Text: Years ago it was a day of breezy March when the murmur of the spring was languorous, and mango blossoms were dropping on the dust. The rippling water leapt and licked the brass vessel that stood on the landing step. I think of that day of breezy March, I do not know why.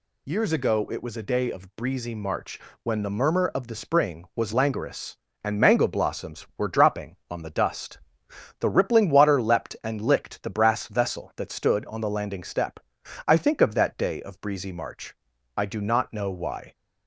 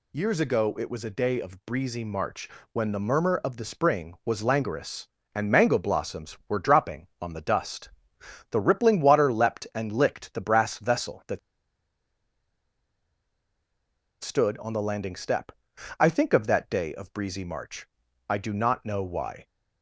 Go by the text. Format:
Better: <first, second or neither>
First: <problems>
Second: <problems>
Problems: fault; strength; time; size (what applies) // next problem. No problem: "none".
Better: first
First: pauses between "March" and "when"; slight; at 2.5 s; 0.24 s long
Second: pauses between "March" and "when"; slight; at 2.4 s; 0.24 s long // pauses between "that" and "stood"; strong; at 11.3 s; 2.8 s long